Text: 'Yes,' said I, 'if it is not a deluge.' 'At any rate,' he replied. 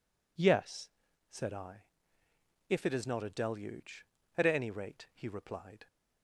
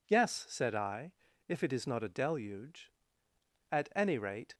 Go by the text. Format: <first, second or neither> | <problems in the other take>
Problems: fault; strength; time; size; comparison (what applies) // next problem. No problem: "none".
first | stops before "he replied"; at 4.5 s